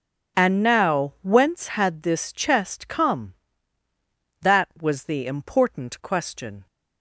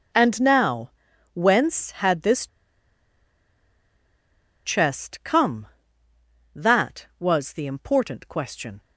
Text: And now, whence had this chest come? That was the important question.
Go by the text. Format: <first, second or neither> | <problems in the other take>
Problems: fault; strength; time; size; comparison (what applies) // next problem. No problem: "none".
first | pauses between "this" and "chest"; strong; at 2.4 s; 2.1 s long